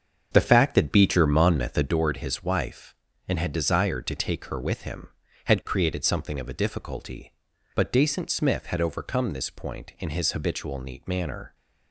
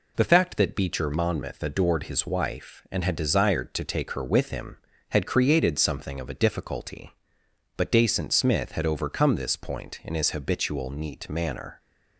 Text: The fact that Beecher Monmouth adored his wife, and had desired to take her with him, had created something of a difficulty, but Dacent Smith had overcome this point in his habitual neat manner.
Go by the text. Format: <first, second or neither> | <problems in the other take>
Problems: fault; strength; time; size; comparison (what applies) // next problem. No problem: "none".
second | starts louder than the rest; until 1.9 s; 7 dB